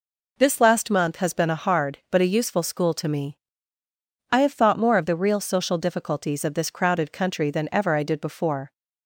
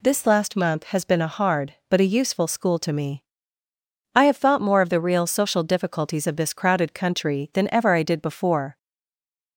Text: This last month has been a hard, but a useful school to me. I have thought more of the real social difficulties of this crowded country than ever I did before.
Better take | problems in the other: first | stays silent after the last word; slight; from 8.7 s on; 0.8 s long

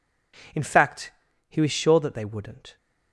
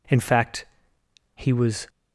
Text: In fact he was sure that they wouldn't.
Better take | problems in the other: first | pauses between "fact" and "he"; noticeable; at 0.6 s; 0.68 s long; also in the first // stops before "sure that they wouldn't"; at 1.8 s

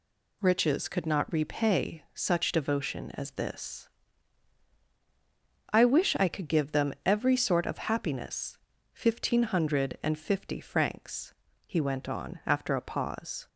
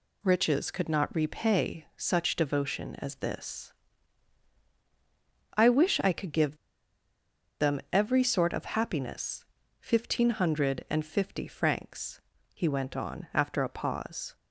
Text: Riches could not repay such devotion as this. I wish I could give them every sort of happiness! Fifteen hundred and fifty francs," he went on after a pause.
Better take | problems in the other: first | pauses between "give" and "them"; at 6.5 s; 1.0 s long

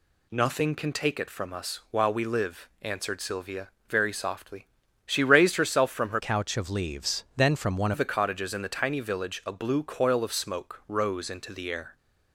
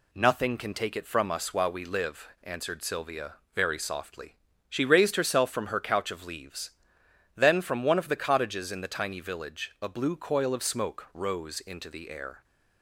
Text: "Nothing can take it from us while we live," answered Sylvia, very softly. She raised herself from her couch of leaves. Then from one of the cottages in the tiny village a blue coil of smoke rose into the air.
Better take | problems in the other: second | changes voice from "couch" to "one"; from 6.1 to 7.9 s; 1.8 s long

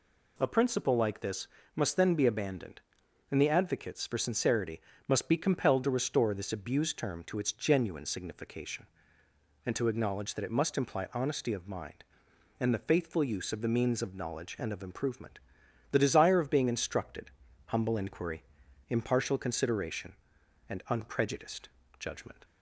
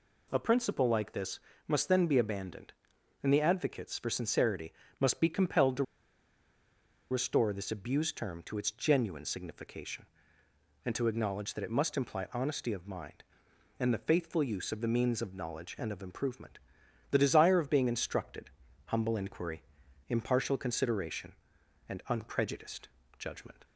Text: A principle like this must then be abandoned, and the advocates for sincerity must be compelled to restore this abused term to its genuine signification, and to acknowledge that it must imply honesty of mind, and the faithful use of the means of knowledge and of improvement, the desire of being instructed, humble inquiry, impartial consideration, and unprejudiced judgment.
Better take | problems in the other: first | pauses between "this" and "must"; slight; at 1.4 s; 0.26 s long; slight in the first // pauses between "sincerity" and "must"; slight; at 4.7 s; 0.26 s long; slight in the first // pauses between "to" and "restore"; strong; at 5.8 s; 1.2 s long // pauses between "unprejudiced" and "judgment"; slight; at 22.8 s; 0.32 s long; slight in the first

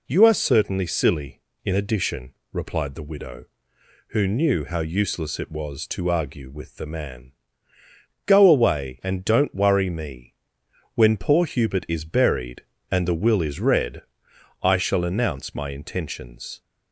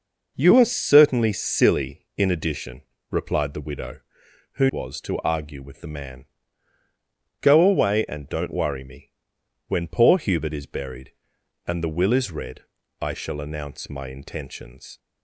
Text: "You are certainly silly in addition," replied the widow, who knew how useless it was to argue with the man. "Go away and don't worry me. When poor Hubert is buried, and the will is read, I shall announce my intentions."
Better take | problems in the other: first | skips "knew how useless it"; at 4.6 s

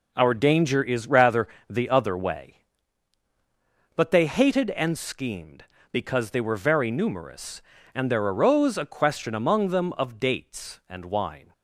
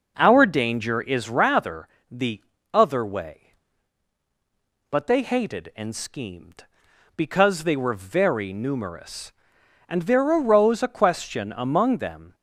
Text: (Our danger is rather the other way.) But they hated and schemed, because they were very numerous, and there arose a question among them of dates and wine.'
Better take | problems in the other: first | pauses between "rather" and "the"; slight; at 1.8 s; 0.22 s long; slight in the first // pauses between "the" and "other"; slight; at 2.4 s; 0.32 s long // stops before "of dates and wine"; at 12.3 s

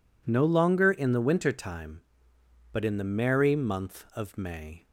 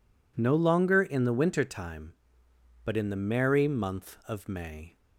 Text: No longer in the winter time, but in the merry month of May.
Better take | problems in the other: neither | none

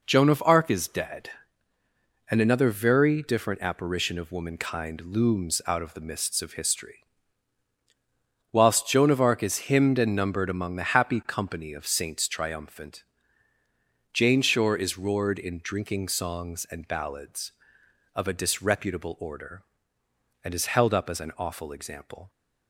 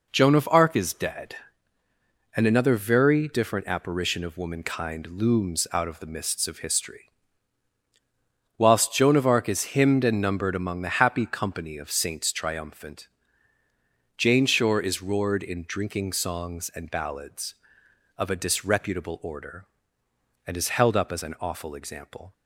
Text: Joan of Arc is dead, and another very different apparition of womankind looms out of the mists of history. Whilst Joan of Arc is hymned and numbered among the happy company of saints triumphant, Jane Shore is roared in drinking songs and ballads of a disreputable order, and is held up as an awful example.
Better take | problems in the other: neither | none

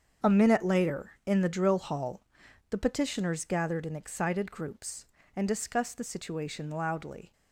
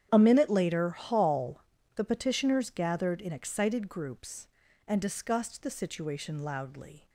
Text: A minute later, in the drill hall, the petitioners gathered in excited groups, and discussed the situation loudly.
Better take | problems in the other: first | starts louder than the rest; strong; until 1.1 s; 9 dB; strong in the first // skips "in the drill"; at 0.8 s

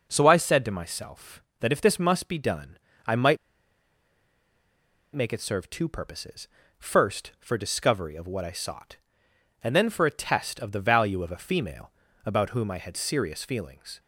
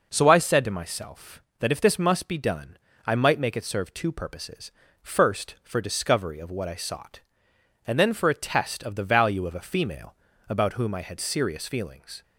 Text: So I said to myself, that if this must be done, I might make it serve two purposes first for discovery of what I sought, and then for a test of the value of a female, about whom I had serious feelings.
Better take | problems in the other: second | pauses between "might" and "make"; strong; at 3.3 s; 1.7 s long // pauses between "purposes" and "first"; slight; at 6.4 s; 0.30 s long; slight in the second

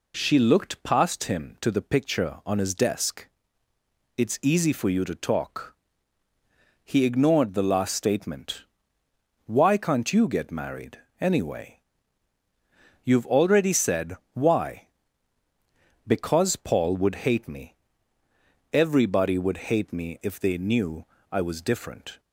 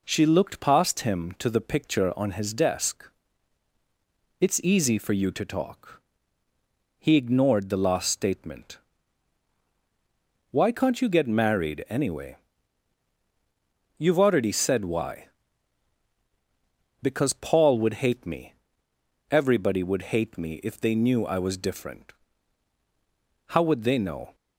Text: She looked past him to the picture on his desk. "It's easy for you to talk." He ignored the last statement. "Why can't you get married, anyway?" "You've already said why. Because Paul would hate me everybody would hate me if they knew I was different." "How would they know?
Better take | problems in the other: second | pauses between "said" and "why"; slight; at 14.1 s; 0.16 s long // pauses between "me" and "everybody"; noticeable; at 17.7 s; 0.98 s long; noticeable in the second // pauses between "knew" and "I"; slight; at 21.0 s; 0.26 s long // stops before "How would they know"; at 22.1 s

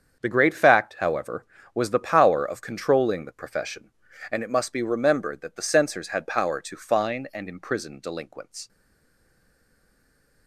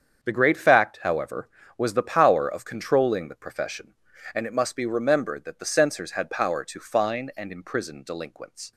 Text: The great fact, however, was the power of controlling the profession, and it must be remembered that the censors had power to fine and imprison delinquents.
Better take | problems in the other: second | starts louder than the rest; strong; until 1.2 s; 7.5 dB; strong in the second // stays silent after the last word; noticeable; from 8.6 s on; 1.8 s long

